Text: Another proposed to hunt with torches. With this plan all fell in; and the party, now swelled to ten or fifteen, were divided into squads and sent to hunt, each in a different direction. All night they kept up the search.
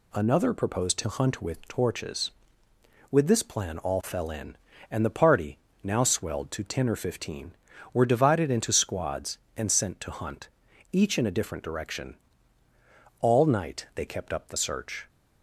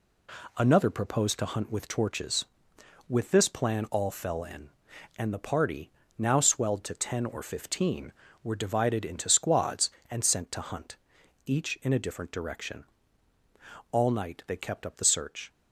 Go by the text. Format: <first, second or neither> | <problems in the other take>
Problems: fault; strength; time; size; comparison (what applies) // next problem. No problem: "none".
neither | none